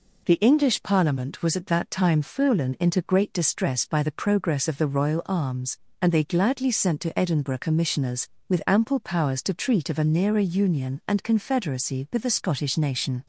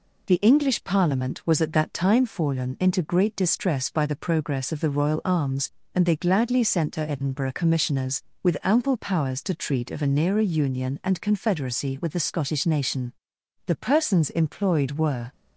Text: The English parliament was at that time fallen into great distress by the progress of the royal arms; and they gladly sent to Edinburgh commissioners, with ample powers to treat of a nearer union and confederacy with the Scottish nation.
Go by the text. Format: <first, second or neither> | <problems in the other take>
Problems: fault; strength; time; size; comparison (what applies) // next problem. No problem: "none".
first | goes on to say "The persons employed were"; from 13.6 s on; 1.6 s long